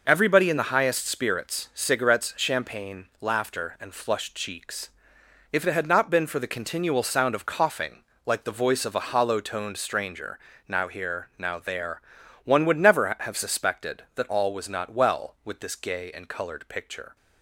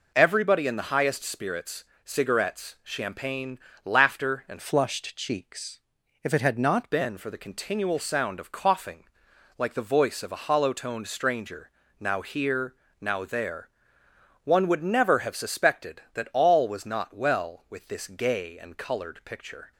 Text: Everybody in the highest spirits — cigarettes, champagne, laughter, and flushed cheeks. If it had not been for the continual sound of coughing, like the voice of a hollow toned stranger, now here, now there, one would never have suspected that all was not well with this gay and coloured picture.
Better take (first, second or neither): first